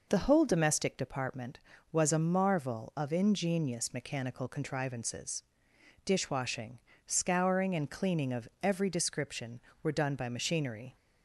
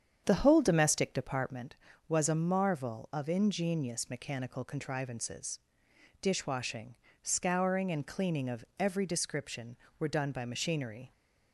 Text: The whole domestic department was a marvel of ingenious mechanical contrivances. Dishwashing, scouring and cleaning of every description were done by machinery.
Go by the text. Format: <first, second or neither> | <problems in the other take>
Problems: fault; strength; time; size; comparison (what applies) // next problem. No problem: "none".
first | starts louder than the rest; strong; until 1.6 s; 8 dB // pauses between "of" and "every"; slight; at 8.6 s; 0.16 s long; slight in the first